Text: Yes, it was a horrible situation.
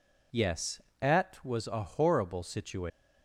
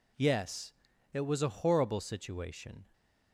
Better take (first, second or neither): second